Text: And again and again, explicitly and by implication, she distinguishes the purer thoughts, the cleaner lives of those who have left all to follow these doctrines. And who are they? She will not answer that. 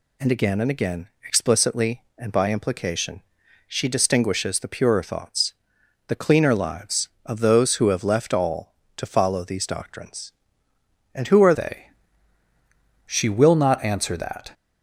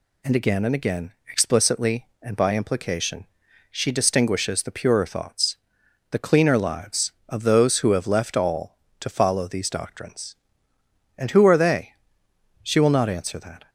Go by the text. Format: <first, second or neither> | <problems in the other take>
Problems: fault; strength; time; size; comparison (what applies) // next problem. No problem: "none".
second | changes voice at "they"; from 11.5 s on; 3.0 s long